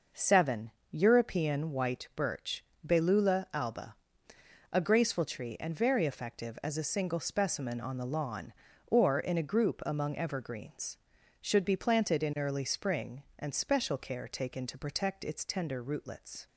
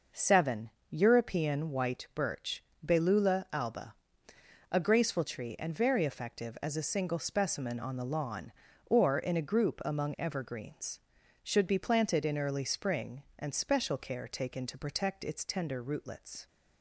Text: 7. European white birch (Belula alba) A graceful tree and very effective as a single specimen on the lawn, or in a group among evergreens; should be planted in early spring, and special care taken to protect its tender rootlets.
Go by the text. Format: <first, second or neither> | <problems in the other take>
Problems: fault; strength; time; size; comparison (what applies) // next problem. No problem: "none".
neither | none